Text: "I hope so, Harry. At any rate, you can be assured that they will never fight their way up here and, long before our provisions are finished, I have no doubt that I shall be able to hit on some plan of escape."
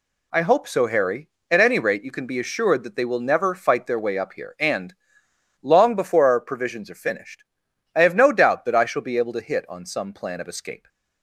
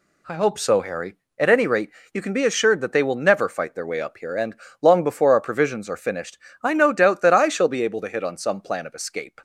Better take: first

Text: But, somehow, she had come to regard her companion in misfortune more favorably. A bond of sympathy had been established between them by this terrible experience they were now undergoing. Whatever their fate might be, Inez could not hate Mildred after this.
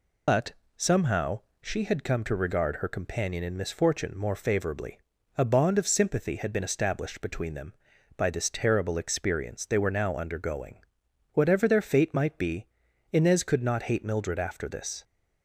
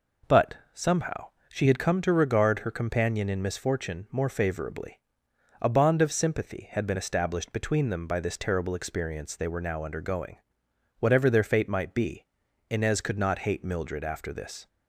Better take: second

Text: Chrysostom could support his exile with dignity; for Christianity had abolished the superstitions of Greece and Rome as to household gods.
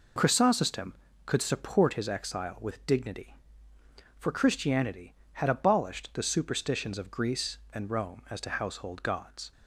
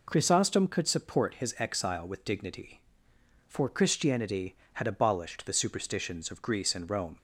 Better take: first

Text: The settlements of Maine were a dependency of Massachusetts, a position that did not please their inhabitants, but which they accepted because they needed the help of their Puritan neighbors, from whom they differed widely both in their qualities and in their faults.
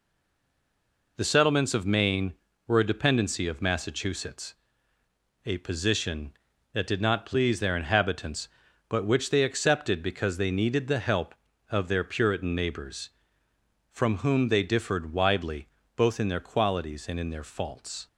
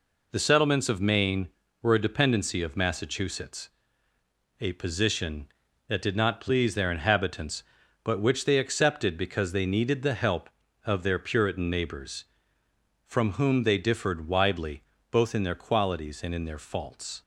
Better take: second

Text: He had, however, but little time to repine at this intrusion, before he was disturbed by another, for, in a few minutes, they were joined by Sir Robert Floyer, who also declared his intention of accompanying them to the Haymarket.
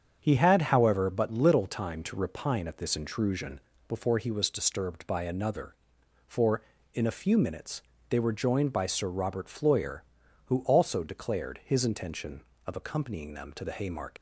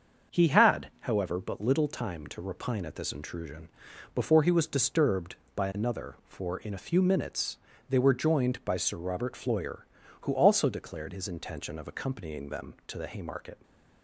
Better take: second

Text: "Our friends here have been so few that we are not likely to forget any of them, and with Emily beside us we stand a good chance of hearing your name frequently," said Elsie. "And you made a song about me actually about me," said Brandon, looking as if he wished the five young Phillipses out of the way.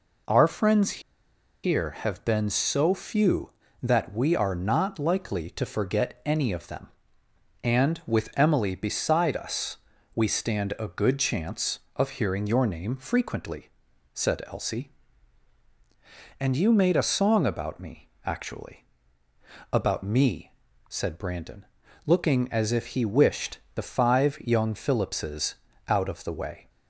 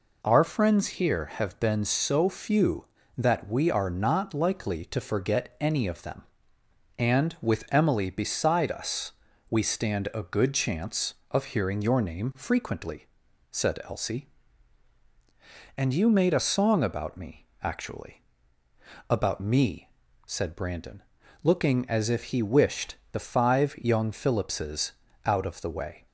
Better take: second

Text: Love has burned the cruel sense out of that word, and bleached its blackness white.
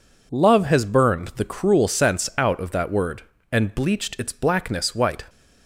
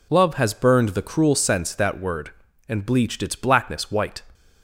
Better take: first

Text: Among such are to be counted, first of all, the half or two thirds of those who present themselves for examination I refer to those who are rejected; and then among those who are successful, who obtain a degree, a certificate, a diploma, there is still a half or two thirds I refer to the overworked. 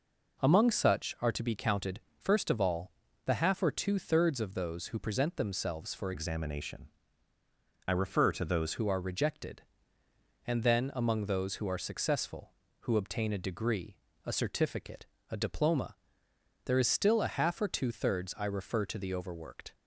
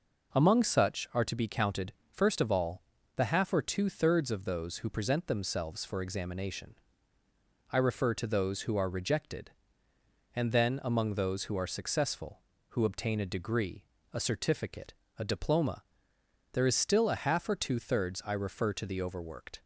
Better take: second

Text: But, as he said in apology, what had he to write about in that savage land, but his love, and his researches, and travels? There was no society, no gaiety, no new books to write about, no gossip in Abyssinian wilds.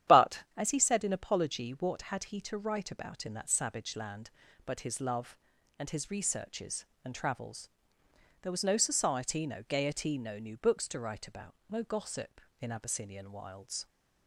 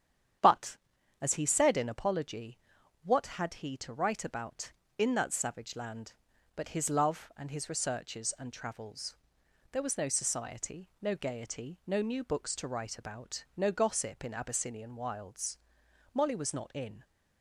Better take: first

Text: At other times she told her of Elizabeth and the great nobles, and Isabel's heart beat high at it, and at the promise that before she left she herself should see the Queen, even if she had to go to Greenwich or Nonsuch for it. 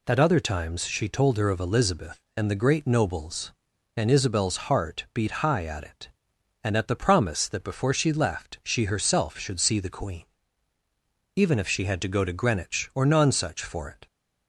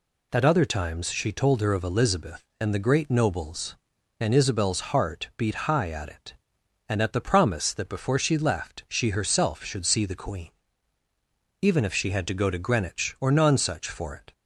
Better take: neither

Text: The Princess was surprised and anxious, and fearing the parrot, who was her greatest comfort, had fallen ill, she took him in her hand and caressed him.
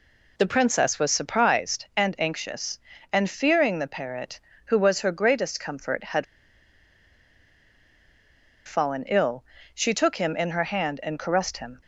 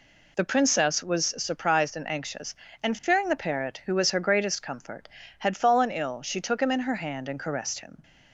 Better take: second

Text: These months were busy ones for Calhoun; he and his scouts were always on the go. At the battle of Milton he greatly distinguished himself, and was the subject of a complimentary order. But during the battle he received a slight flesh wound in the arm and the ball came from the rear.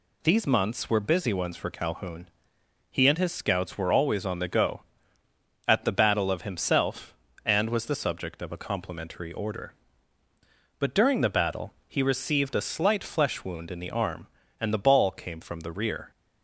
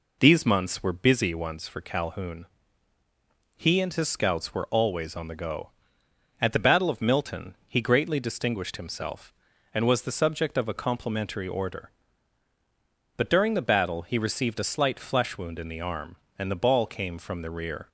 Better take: second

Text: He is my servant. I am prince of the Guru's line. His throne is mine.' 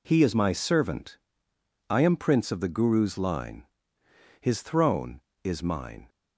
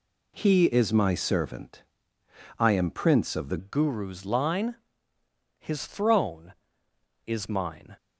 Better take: first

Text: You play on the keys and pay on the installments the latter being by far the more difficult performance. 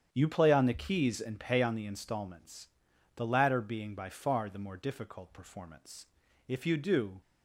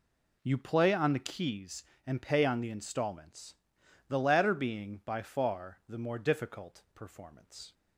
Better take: second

